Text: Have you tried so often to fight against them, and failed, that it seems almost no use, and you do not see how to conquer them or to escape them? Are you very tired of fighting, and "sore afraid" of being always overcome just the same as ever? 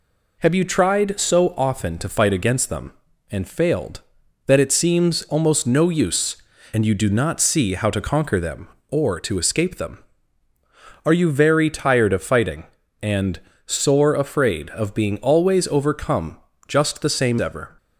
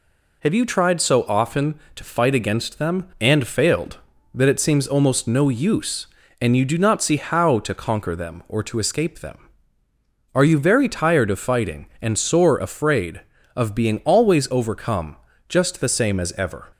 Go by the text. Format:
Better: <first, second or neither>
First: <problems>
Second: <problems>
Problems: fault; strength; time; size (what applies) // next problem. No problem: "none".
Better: second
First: pauses between "and" and "sore"; slight; at 13.3 s; 0.26 s long // pauses between "overcome" and "just"; slight; at 16.3 s; 0.30 s long // skips "as"; at 17.3 s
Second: pauses between "overcome" and "just"; slight; at 15.1 s; 0.32 s long